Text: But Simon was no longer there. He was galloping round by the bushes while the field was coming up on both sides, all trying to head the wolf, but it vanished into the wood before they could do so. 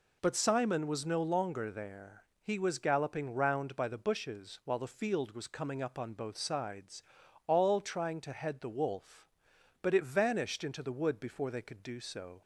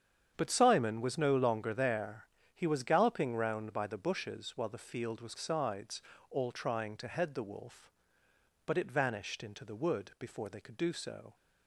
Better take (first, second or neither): first